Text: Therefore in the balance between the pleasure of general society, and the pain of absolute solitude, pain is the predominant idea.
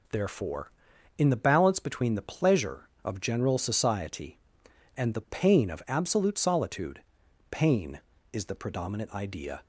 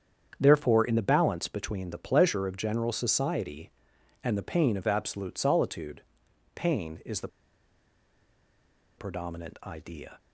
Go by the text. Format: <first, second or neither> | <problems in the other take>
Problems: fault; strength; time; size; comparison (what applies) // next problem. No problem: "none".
first | starts louder than the rest; strong; until 1.4 s; 8 dB // pauses between "the" and "predominant"; strong; at 7.2 s; 1.6 s long